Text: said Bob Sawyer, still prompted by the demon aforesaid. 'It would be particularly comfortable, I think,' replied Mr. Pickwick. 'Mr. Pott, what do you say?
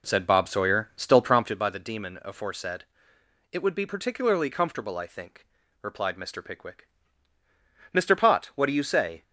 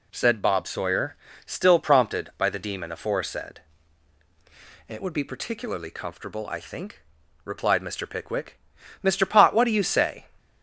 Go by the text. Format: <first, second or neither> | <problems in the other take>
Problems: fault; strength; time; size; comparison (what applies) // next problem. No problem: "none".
second | starts louder than the rest; until 1.7 s; 3.5 dB